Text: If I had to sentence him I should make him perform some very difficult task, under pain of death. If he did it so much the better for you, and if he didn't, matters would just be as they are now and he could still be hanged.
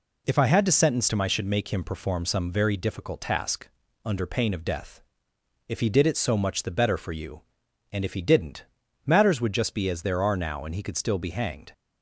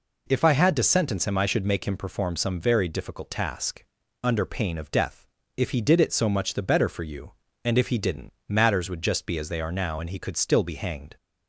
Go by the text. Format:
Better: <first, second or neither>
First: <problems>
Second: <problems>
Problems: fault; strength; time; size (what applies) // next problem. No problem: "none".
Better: second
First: says "there" for "they"; at 10.0 s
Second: none